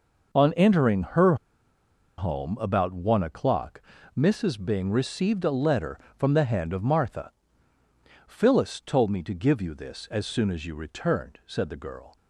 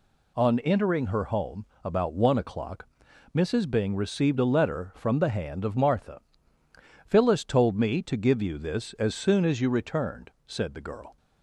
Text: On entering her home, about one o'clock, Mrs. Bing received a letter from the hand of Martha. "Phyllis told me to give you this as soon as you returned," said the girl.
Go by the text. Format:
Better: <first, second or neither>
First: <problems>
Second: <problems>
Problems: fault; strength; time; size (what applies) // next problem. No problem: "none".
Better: second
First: pauses between "her" and "home"; noticeable; at 1.3 s; 0.82 s long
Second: none